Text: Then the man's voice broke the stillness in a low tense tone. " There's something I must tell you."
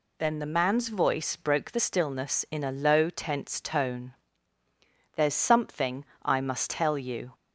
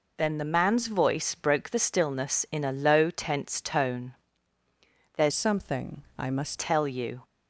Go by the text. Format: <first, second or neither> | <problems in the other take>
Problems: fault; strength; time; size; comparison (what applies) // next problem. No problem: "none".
first | changes voice from "something" to "must"; from 5.3 to 6.5 s; 1.2 s long // pauses between "something" and "I"; slight; at 6.0 s; 0.16 s long; slight in the first